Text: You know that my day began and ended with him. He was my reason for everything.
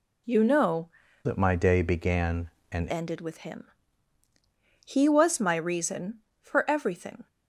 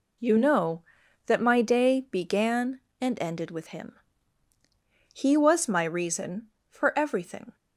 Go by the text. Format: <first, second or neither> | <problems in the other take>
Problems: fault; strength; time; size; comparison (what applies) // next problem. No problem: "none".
second | changes voice from "that" to "and"; from 1.2 to 2.8 s; 1.6 s long